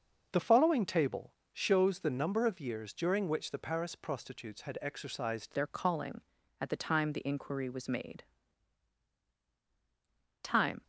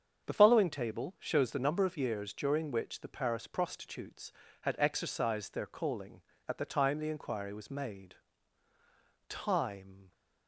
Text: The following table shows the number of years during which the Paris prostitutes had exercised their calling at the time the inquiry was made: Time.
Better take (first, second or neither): second